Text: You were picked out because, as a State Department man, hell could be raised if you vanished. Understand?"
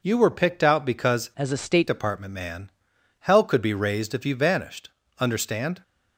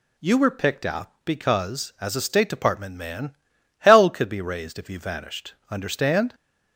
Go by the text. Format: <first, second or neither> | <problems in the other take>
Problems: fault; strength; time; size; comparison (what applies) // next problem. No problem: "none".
second | changes voice from "as" to "State"; from 1.3 to 1.8 s; 0.5 s long